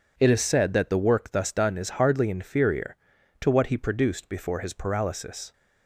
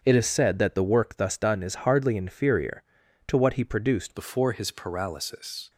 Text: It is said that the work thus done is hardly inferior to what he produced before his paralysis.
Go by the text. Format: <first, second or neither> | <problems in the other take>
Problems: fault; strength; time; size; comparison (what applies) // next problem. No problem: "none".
first | starts louder than the rest; until 1.0 s; 7 dB // changes voice at "before"; from 4.1 s on; 1.5 s long